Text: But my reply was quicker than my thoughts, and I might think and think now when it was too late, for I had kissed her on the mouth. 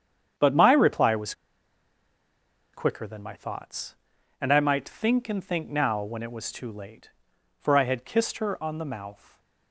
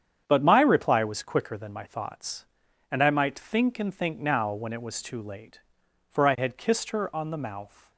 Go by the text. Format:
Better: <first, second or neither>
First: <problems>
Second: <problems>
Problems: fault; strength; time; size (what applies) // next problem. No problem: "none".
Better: second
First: starts louder than the rest; strong; until 2.8 s; 8.5 dB // pauses between "was" and "quicker"; strong; at 1.3 s; 1.4 s long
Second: starts louder than the rest; strong; until 1.2 s; 8.5 dB